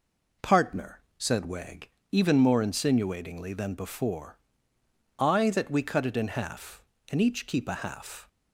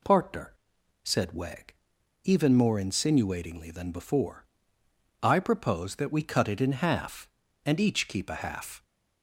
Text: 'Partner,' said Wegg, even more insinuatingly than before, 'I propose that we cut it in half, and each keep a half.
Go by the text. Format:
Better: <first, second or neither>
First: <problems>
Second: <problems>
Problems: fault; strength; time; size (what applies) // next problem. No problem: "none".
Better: second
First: skips "propose"; at 5.4 s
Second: none